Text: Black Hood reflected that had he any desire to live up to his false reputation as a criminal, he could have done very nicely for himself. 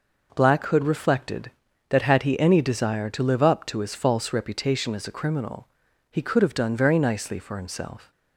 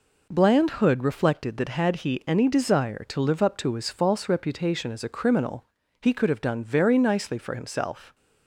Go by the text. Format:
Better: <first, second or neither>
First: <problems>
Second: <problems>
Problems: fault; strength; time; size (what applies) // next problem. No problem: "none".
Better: first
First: none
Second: says "Bland" for "Black"; at 0.3 s